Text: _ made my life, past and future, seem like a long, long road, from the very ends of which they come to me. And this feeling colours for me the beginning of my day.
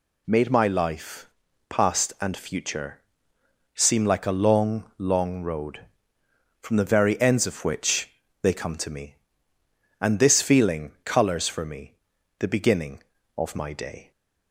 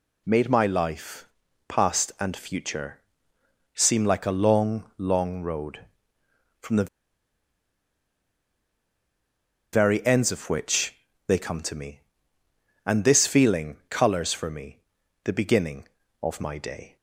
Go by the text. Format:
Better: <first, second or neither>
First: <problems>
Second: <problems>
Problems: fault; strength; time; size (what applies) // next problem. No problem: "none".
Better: first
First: pauses between "which" and "they"; slight; at 8.1 s; 0.32 s long // pauses between "me" and "the"; at 11.9 s; 0.44 s long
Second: pauses between "the" and "very"; strong; at 6.8 s; 2.8 s long // pauses between "which" and "they"; slight; at 10.9 s; 0.32 s long // pauses between "me" and "the"; at 14.7 s; 0.44 s long